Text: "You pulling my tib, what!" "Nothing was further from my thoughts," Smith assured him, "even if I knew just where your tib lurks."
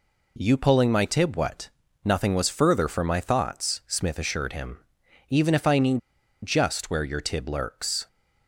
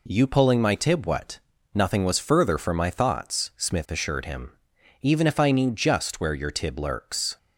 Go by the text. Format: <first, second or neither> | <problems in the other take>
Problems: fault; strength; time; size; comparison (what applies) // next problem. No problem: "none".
second | pauses between "knew" and "just"; at 5.9 s; 0.45 s long